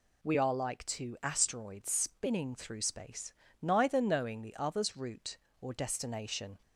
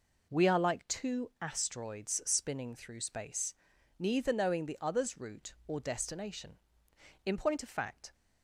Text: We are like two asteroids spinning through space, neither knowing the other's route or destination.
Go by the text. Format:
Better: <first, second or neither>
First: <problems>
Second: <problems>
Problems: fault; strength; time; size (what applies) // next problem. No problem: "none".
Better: first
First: none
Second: goes on to say "In point of fact"; noticeable; from 7.2 s on; 0.88 s long